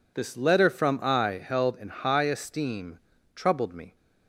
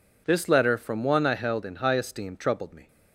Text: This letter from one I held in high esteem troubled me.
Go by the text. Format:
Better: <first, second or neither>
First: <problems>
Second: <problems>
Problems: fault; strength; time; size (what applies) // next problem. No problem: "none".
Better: second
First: skips "one"; at 0.9 s // pauses between "esteem" and "troubled"; slight; at 2.9 s; 0.34 s long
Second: none